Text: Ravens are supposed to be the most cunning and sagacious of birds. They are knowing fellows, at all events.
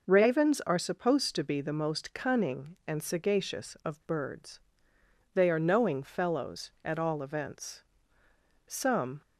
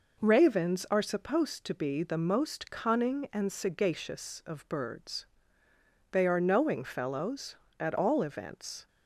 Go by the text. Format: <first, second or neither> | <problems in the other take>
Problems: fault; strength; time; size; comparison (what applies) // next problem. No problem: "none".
second | goes on to say "Some"; from 8.6 s on; 0.54 s long